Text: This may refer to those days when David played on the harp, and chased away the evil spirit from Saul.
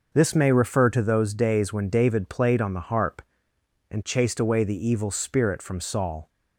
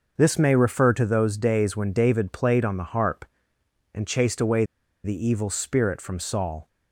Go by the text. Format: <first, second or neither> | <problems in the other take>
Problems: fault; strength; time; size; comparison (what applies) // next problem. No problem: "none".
first | pauses between "away" and "the"; at 4.6 s; 0.40 s long